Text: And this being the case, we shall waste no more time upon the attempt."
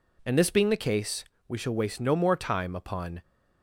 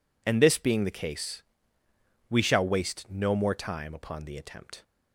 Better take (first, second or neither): second